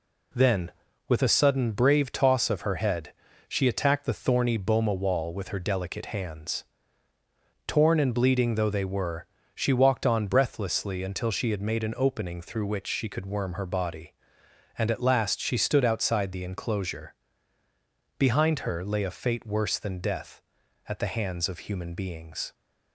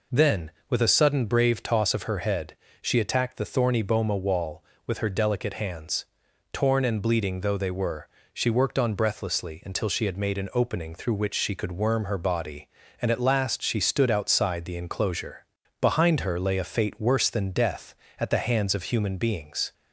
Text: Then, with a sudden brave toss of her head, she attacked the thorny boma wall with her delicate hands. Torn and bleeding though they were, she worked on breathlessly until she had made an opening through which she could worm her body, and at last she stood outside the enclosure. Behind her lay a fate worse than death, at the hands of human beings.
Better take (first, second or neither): second